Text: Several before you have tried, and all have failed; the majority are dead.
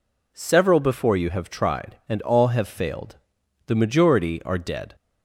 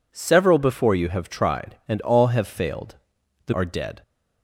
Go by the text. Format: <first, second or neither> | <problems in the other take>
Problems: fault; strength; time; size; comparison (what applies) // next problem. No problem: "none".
first | skips "majority"; at 3.5 s